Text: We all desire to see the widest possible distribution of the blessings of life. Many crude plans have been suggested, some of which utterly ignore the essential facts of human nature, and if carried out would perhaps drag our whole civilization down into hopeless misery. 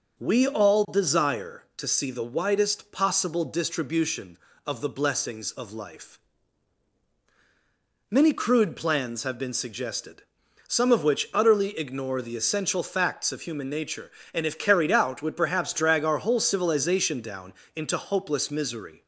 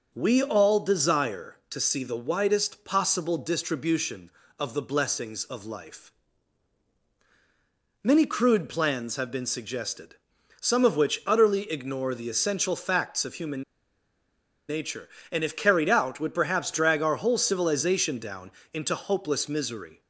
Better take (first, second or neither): first